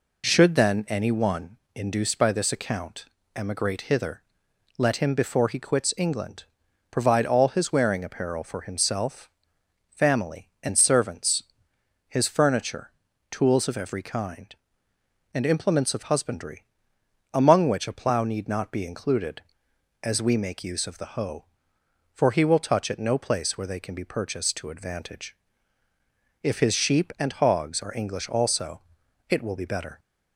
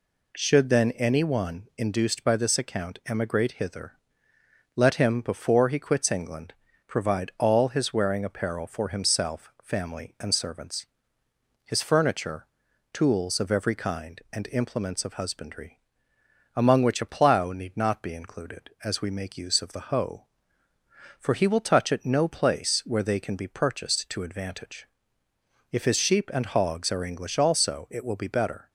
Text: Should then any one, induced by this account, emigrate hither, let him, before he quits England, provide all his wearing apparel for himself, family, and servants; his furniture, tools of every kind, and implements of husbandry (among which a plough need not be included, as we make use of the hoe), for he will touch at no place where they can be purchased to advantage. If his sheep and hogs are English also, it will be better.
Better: neither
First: none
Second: none

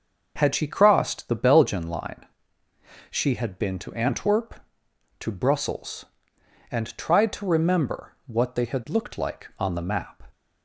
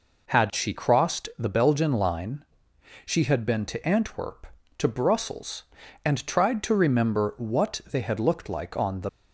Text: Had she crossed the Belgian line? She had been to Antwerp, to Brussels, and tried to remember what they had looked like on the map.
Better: first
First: none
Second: stops before "map"; at 9.0 s

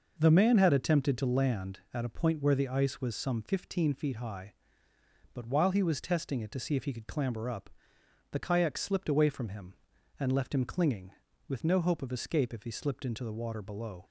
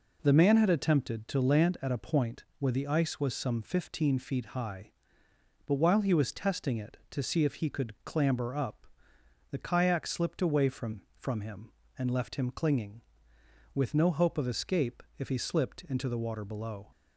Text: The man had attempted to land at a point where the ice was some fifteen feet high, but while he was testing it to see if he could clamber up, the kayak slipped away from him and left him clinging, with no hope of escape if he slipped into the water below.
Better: first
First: none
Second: says "from" twice; at 11.1 s // pauses between "escape" and "if"; slight; at 15.0 s; 0.16 s long

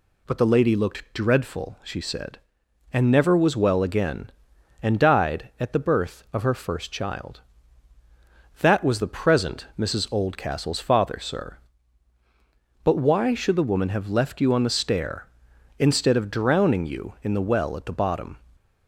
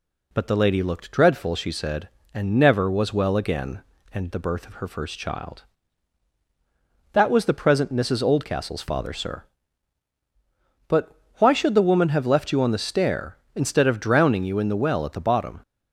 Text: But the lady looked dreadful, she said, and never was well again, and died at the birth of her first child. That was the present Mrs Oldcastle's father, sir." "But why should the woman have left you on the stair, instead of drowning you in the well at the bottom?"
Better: first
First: none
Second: skips "died at"; at 4.3 s // pauses between "But" and "why"; slight; at 11.1 s; 0.24 s long

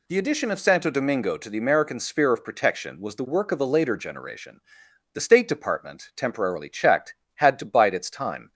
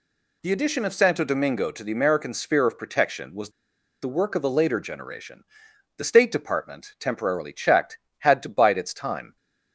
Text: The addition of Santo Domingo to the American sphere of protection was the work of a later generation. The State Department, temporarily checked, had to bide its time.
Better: first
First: none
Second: pauses between "was" and "the"; noticeable; at 3.4 s; 0.52 s long

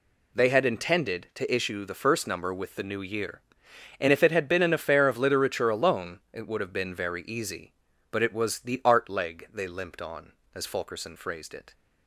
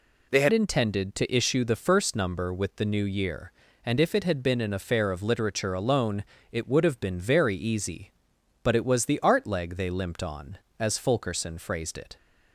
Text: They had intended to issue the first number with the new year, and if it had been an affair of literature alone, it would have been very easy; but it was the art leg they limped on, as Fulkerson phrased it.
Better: first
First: none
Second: changes voice at "intended"; from 0.5 s on; 11.6 s long

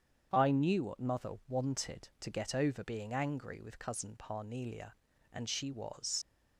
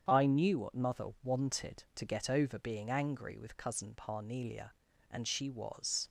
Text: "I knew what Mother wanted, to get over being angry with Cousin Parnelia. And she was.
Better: second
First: starts louder than the rest; strong; until 1.3 s; 8 dB // leaves "was" unfinished; at 6.2 s; 65 ms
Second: starts louder than the rest; strong; until 1.0 s; 8 dB

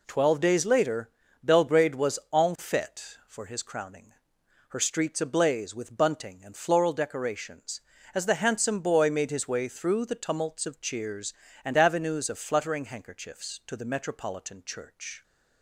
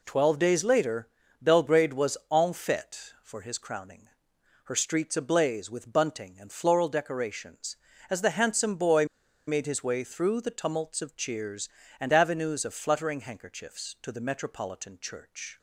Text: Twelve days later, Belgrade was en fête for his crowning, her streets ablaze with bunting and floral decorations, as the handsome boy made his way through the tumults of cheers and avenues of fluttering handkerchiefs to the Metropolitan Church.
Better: first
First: none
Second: pauses between "boy" and "made"; at 9.0 s; 0.42 s long

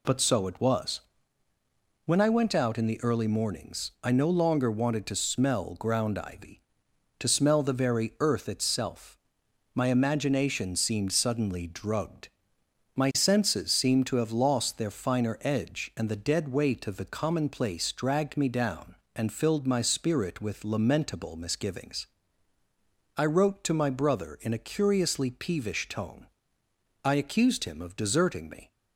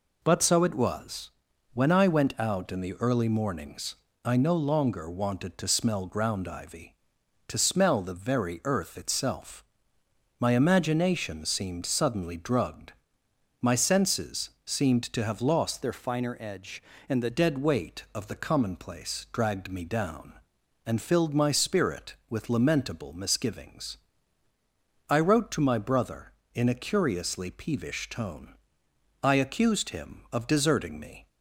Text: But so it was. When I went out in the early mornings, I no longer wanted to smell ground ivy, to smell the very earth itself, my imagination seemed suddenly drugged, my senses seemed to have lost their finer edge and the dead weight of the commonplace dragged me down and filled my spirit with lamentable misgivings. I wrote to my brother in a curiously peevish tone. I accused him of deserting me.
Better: first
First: none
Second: pauses between "senses" and "seemed"; slight; at 14.4 s; 0.16 s long // changes voice from "their" to "the"; from 15.8 to 17.3 s; 1.5 s long

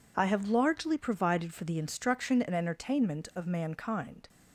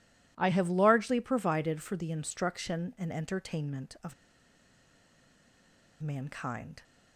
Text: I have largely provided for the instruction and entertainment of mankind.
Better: first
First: none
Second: pauses between "of" and "mankind"; strong; at 4.1 s; 1.8 s long

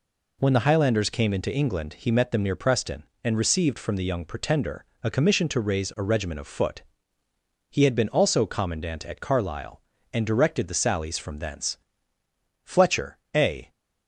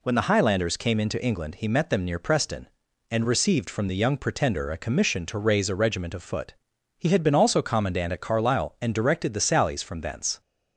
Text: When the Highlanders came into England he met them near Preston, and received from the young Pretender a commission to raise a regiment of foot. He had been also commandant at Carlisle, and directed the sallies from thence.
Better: second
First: pauses between "Pretender" and "a"; slight; at 4.8 s; 0.18 s long // goes on to say "Fletcher a"; noticeable; from 12.6 s on; 1.0 s long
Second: none

